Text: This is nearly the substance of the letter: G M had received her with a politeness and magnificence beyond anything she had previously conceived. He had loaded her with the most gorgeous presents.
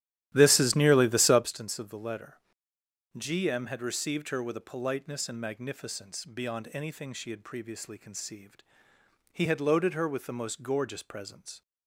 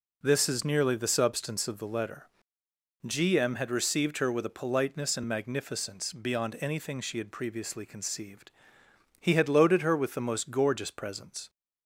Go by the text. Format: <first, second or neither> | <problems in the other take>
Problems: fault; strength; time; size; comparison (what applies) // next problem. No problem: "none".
second | starts louder than the rest; strong; until 1.5 s; 13 dB